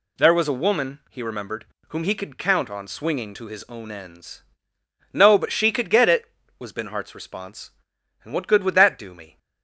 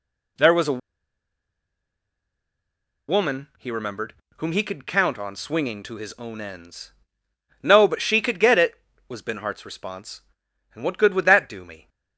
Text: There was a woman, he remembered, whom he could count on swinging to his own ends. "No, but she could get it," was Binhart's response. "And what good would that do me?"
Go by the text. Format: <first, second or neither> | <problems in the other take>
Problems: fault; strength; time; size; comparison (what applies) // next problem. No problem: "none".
first | pauses between "a" and "woman"; strong; at 0.7 s; 2.3 s long